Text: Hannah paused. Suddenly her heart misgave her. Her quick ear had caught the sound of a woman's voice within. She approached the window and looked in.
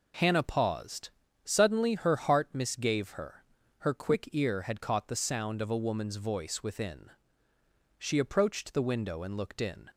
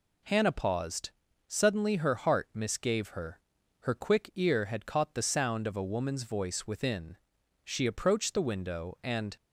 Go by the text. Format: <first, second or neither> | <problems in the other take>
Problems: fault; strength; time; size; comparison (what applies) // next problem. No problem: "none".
first | stops before "looked in"; at 9.3 s